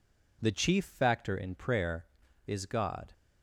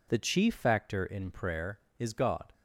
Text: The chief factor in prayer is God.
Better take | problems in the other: neither | none

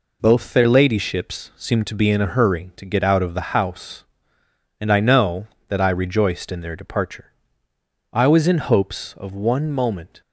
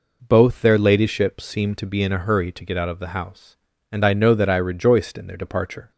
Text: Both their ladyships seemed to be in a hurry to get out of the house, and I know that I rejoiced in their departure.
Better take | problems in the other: second | goes on to say "I was in hopes of one moment"; strong; from 8.1 s on; 2.0 s long

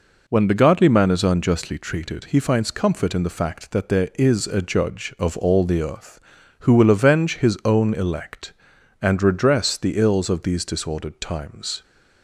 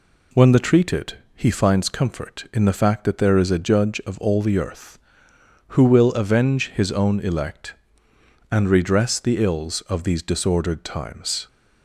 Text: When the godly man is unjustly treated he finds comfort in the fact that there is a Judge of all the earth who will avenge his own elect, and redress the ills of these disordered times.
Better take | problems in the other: first | skips "godly man is unjustly"; at 0.5 s // pauses between "treated" and "he"; slight; at 1.1 s; 0.18 s long

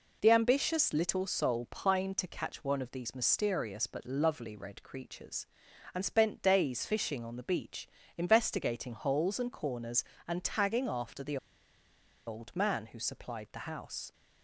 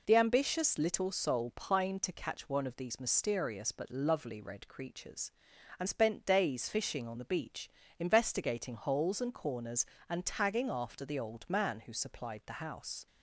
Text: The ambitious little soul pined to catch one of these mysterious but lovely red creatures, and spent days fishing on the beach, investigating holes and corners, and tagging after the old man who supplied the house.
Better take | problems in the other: second | pauses between "the" and "old"; noticeable; at 11.3 s; 0.90 s long

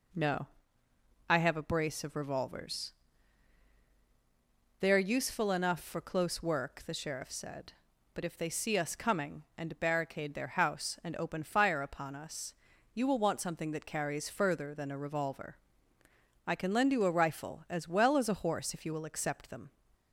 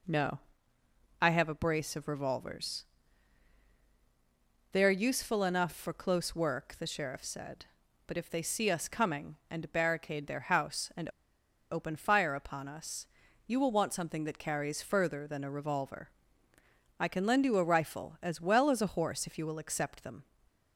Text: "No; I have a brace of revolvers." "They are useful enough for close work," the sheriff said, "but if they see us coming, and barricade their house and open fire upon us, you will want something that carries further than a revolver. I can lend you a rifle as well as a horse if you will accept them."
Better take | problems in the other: first | pauses between "and" and "open"; noticeable; at 11.0 s; 0.62 s long

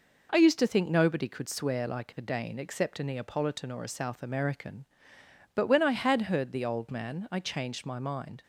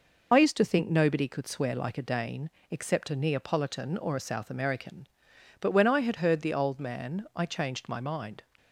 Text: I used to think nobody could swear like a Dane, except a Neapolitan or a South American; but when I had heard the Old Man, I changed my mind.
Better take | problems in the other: first | loses the start of "I"; at 0.3 s; 55 ms

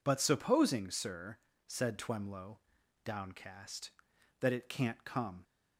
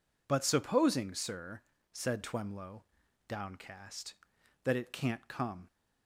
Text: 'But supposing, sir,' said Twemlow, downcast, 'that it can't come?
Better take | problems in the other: neither | none

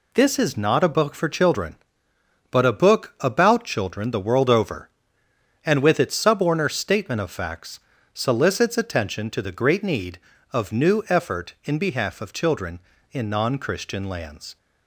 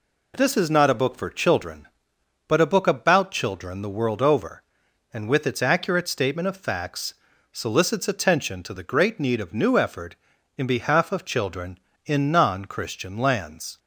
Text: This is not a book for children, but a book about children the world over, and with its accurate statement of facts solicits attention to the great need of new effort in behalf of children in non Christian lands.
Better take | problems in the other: second | says "suborner" for "accurate"; at 6.1 s // pauses between "facts" and "solicits"; slight; at 7.8 s; 0.32 s long; also in the second

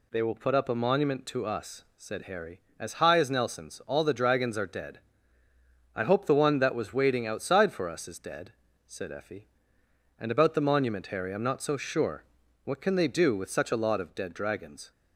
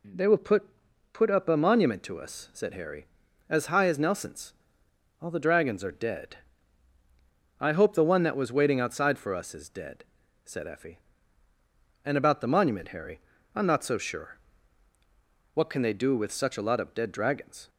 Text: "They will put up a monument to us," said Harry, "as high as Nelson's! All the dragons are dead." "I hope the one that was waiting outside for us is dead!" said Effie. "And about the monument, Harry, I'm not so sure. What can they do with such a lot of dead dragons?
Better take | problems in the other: first | says "put" twice; at 1.1 s

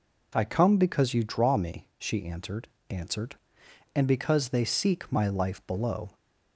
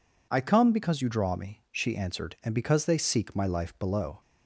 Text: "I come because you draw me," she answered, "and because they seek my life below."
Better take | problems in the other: second | says "answered" twice; at 2.8 s

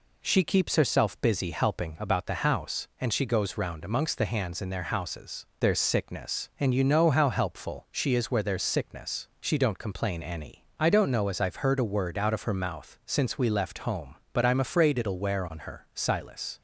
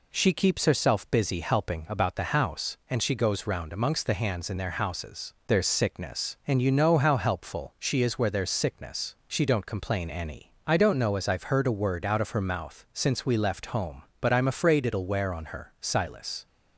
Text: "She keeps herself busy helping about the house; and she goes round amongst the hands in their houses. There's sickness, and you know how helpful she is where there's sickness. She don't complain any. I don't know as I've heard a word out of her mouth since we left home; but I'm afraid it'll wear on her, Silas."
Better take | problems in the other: neither | none

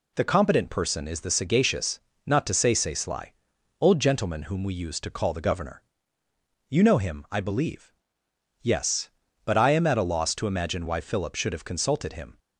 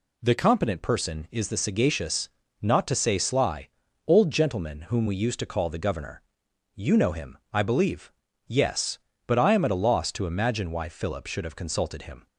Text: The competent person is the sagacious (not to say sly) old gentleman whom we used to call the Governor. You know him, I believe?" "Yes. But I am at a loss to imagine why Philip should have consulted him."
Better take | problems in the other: second | says "say" twice; at 2.7 s

